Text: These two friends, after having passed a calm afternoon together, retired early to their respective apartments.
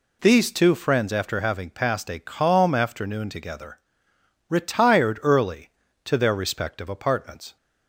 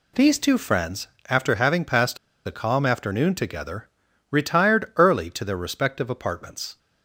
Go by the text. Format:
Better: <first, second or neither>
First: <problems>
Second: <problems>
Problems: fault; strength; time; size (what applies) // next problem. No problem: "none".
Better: first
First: none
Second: pauses between "passed" and "a"; slight; at 2.1 s; 0.30 s long